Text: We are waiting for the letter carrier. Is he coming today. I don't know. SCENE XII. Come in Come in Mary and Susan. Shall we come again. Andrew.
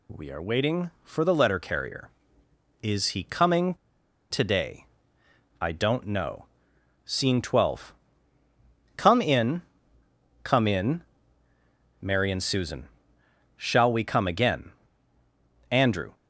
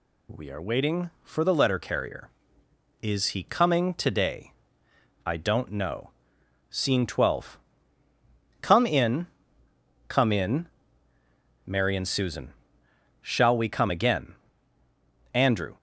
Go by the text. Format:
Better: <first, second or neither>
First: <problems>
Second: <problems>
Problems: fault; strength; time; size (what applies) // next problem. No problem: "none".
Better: second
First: pauses between "coming" and "today"; noticeable; at 3.7 s; 0.55 s long // pauses between "in" and "Come"; noticeable; at 9.6 s; 0.82 s long // pauses between "in" and "Mary"; noticeable; at 11.0 s; 0.98 s long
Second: pauses between "in" and "Come"; noticeable; at 9.2 s; 0.82 s long // pauses between "in" and "Mary"; noticeable; at 10.6 s; 0.98 s long